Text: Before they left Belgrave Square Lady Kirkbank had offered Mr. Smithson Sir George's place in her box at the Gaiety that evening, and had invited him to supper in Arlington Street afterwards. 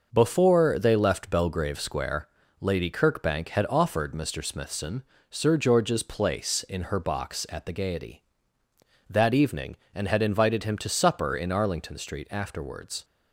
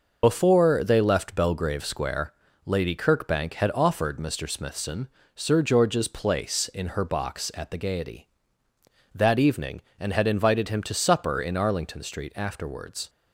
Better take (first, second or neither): first